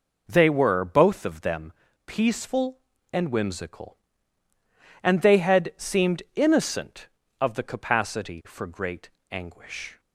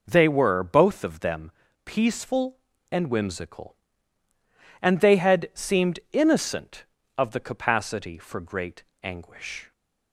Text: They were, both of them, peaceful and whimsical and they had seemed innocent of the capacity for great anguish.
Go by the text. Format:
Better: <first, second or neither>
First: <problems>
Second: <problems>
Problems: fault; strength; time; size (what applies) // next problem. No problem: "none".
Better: neither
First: pauses between "great" and "anguish"; slight; at 9.0 s; 0.22 s long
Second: pauses between "great" and "anguish"; slight; at 8.8 s; 0.20 s long